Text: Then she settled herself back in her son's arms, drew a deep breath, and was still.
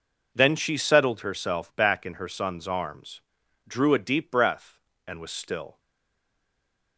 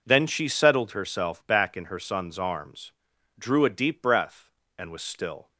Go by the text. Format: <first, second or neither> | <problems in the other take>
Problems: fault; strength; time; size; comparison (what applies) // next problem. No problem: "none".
second | stays silent after the last word; noticeable; from 5.7 s on; 1.2 s long